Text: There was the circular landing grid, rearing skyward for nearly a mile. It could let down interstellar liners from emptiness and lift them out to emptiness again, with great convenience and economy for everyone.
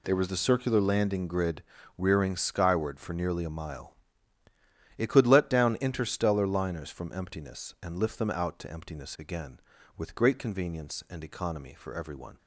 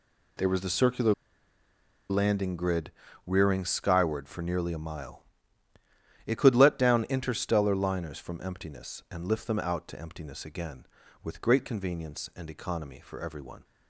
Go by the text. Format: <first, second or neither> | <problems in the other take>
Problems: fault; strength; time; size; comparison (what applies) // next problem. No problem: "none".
first | pauses between "circular" and "landing"; noticeable; at 1.1 s; 0.97 s long